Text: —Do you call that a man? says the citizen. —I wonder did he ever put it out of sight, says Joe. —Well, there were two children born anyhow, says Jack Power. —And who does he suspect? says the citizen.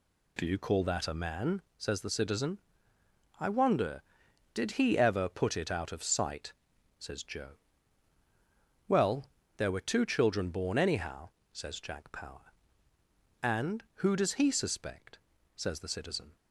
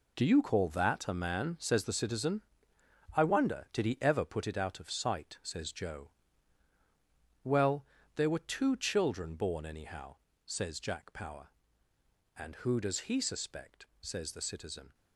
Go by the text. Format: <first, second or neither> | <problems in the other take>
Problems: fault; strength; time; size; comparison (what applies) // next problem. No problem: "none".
first | gets quieter; strong; throughout; 10.5 dB